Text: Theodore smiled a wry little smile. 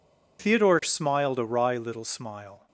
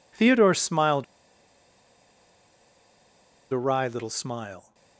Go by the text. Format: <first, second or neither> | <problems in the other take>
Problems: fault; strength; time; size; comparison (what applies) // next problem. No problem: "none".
first | pauses between "smiled" and "a"; strong; at 1.0 s; 2.4 s long